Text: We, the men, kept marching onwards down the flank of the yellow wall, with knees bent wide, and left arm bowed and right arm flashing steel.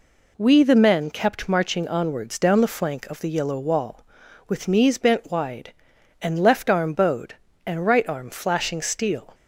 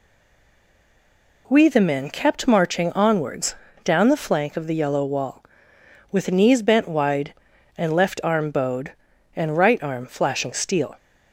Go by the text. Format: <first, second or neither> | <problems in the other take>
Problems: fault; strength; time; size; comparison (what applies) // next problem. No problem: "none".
first | stays silent before the first word; noticeable; until 1.4 s; 1.4 s long // pauses between "onwards" and "down"; slight; at 3.5 s; 0.28 s long